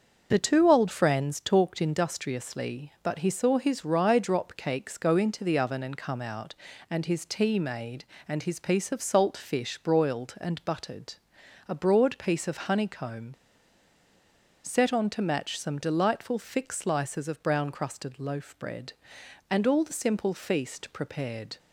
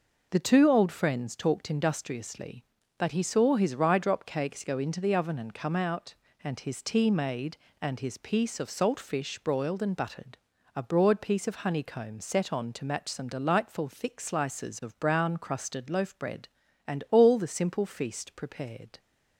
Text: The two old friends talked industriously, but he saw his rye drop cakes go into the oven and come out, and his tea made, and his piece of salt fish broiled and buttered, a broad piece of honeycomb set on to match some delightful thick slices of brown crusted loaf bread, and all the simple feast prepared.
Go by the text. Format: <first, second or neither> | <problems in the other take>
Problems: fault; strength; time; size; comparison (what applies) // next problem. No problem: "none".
second | starts louder than the rest; until 1.3 s; 6.5 dB // pauses between "honeycomb" and "set"; strong; at 13.3 s; 1.3 s long